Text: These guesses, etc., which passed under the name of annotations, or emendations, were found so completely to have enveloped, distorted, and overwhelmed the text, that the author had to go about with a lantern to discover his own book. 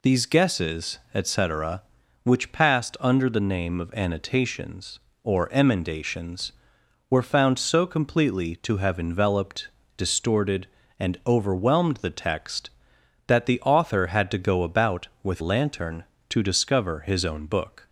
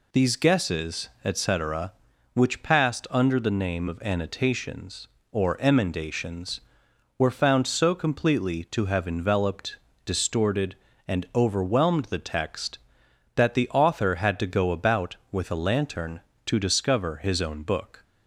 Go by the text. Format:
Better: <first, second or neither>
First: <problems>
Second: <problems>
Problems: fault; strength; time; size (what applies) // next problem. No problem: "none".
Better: second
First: skips "a"; at 15.4 s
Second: none